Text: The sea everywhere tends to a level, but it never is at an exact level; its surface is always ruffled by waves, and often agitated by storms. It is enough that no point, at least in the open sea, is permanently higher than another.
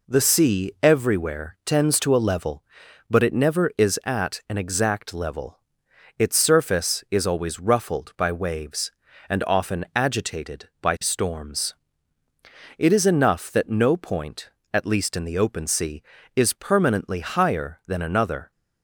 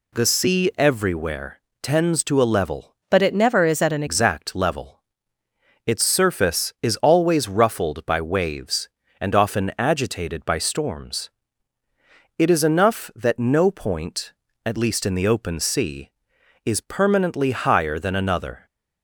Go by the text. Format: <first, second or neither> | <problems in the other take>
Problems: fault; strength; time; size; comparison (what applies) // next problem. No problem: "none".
first | pauses between "everywhere" and "tends"; slight; at 1.5 s; 0.24 s long // changes voice from "but" to "an"; from 3.1 to 4.0 s; 0.9 s long